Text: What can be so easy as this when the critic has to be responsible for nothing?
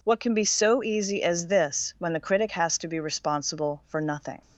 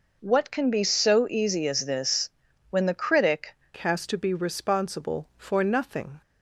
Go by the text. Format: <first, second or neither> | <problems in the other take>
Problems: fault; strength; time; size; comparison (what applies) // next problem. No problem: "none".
first | pauses between "this" and "when"; at 2.3 s; 0.40 s long // changes voice at "has"; from 3.7 s on; 2.5 s long